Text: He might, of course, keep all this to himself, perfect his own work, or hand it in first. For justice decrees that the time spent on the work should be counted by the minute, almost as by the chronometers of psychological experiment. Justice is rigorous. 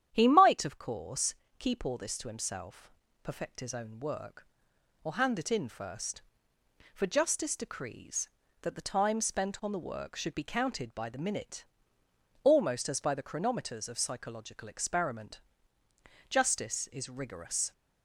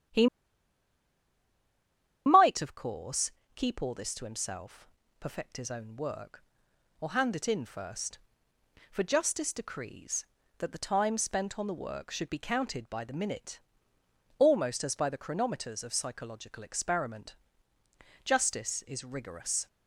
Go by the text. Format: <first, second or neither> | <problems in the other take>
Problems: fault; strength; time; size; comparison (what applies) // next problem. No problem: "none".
first | starts louder than the rest; strong; until 3.1 s; 10 dB; strong in the first // pauses between "He" and "might"; strong; at 0.2 s; 2.0 s long